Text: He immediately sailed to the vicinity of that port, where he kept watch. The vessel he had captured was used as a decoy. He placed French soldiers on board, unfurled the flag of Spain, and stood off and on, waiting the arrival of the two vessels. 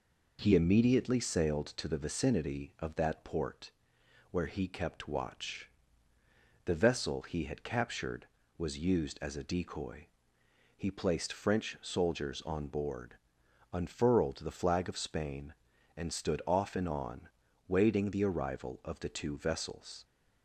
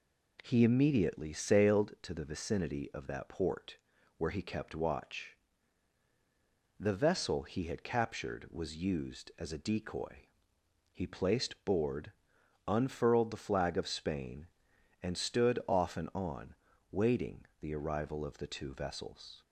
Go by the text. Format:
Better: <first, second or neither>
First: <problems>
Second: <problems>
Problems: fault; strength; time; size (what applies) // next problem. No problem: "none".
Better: first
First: none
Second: skips "French soldiers on"; at 11.6 s // pauses between "waiting" and "the"; slight; at 17.4 s; 0.16 s long